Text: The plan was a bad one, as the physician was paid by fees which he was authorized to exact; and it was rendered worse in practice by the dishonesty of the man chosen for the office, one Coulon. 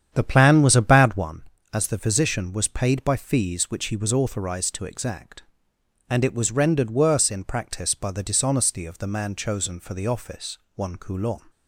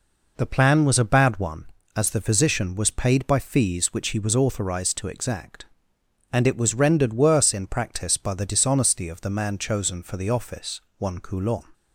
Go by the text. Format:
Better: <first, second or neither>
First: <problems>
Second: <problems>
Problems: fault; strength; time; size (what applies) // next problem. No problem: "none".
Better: second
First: starts louder than the rest; strong; until 1.4 s; 8.5 dB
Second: none